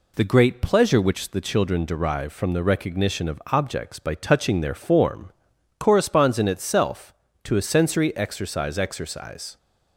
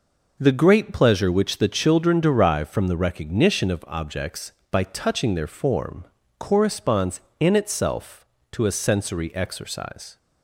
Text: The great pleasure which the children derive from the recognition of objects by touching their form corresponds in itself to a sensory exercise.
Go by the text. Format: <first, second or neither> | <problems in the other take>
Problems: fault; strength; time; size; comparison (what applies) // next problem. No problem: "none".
second | pauses between "form" and "corresponds"; at 5.3 s; 0.44 s long; slight in the second // says "exercise" twice; at 8.7 s